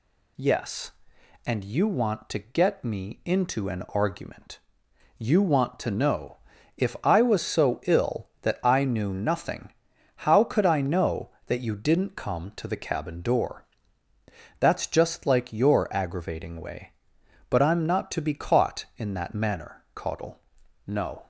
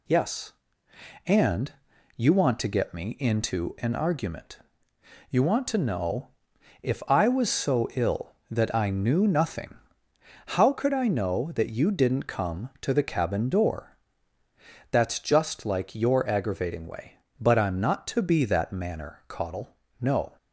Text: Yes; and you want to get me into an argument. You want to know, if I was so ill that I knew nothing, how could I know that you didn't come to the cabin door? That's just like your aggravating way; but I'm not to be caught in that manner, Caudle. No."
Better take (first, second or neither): first